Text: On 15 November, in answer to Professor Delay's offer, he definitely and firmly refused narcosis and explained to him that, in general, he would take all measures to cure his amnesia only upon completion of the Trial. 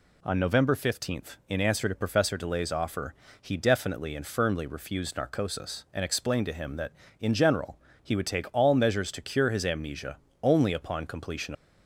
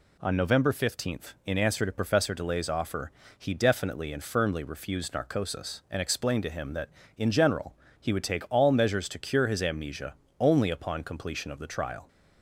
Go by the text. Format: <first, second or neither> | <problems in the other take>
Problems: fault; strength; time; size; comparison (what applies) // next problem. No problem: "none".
second | pauses between "amnesia" and "only"; slight; at 10.1 s; 0.24 s long; slight in the second // stops before "of the Trial"; at 11.5 s